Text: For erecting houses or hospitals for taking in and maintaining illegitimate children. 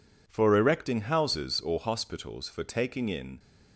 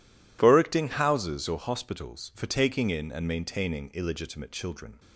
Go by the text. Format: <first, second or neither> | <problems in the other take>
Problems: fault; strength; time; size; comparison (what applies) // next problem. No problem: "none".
second | stops before "and maintaining illegitimate children"; at 3.3 s